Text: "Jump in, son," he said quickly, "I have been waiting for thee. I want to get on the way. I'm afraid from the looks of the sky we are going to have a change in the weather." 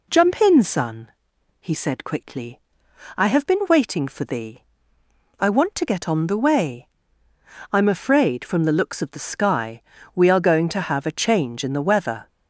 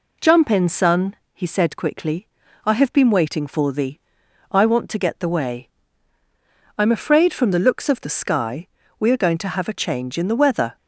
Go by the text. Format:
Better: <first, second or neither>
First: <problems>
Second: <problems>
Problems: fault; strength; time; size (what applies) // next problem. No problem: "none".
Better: first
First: pauses between "sky" and "we"; slight; at 9.8 s; 0.34 s long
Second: skips "on"; at 5.2 s // pauses between "sky" and "we"; slight; at 8.6 s; 0.32 s long